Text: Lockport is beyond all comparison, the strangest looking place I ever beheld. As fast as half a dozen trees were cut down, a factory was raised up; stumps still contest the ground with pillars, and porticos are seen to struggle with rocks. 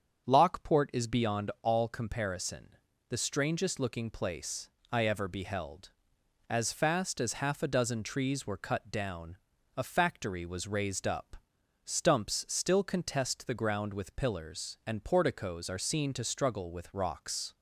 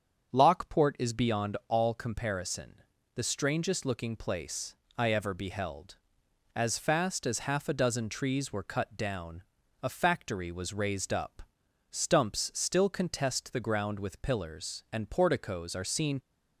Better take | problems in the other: first | starts louder than the rest; strong; until 1.3 s; 7.5 dB; strong in the first // pauses between "place" and "I"; slight; at 4.7 s; 0.24 s long; slight in the first // stops before "to struggle with rocks"; at 16.1 s

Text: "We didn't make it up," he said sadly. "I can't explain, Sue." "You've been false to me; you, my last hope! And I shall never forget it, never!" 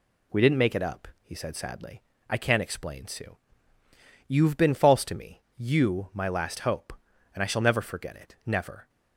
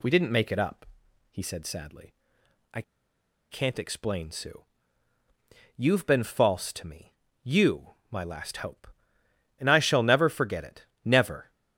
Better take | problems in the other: first | pauses between "I" and "can't"; noticeable; at 2.8 s; 0.69 s long

